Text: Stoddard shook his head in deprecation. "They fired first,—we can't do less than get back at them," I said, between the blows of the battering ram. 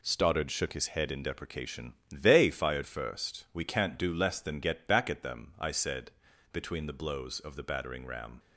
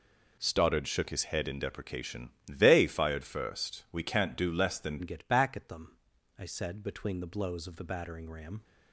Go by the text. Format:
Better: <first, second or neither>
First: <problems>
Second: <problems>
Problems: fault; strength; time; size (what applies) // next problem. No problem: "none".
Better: first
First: none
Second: changes voice at "get"; from 5.0 s on; 3.6 s long